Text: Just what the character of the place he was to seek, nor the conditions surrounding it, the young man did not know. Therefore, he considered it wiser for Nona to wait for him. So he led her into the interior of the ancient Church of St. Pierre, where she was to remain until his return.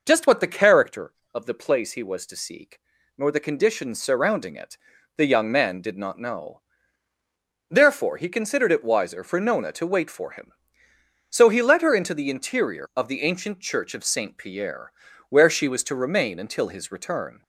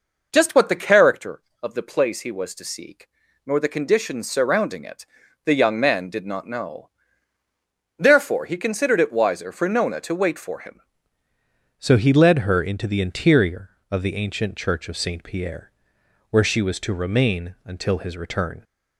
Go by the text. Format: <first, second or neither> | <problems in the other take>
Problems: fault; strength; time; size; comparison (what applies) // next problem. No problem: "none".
first | changes voice at "So"; from 11.7 s on; 6.9 s long